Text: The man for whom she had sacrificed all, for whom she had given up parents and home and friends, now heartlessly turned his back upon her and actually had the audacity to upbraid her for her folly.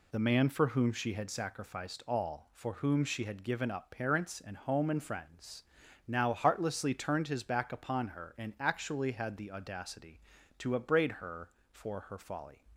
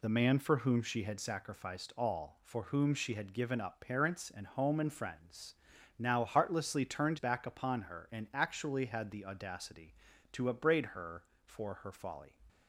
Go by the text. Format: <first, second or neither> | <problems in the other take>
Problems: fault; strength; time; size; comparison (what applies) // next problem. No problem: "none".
first | skips "his"; at 7.1 s